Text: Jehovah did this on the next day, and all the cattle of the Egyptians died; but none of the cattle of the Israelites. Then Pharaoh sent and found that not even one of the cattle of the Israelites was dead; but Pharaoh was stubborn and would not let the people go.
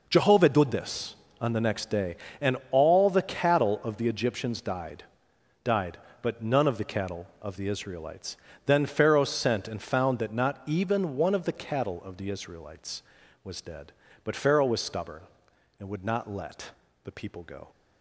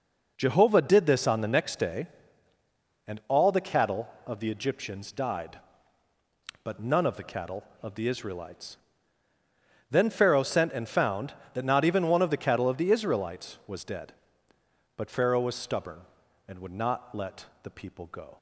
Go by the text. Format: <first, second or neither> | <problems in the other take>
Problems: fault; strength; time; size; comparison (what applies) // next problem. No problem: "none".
second | says "died" twice; at 5.6 s // pauses between "let" and "the"; slight; at 16.7 s; 0.32 s long; slight in the second